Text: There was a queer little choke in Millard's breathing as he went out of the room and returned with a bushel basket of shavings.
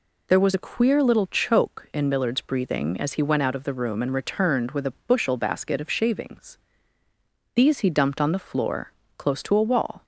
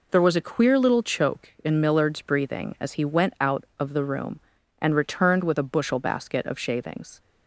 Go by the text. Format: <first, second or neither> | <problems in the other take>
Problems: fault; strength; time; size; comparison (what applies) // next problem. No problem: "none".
second | goes on to say "These he dumped on the floor close to a wall"; strong; from 7.5 s on; 2.4 s long